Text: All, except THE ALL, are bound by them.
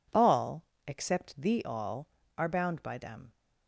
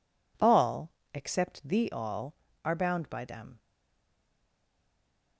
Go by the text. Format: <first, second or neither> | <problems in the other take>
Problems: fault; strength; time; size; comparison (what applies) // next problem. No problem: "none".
first | stays silent after the last word; noticeable; from 3.5 s on; 1.8 s long